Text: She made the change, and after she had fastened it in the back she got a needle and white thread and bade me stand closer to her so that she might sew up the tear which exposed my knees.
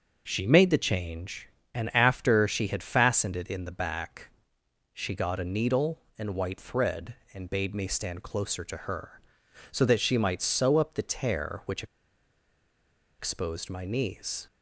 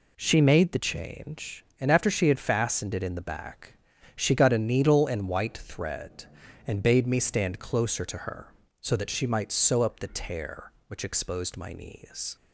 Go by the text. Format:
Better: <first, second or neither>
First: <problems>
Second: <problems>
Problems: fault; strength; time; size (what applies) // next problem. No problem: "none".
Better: second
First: pauses between "back" and "she"; noticeable; at 4.3 s; 0.62 s long // pauses between "which" and "exposed"; strong; at 11.8 s; 1.3 s long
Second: pauses between "back" and "she"; at 3.7 s; 0.36 s long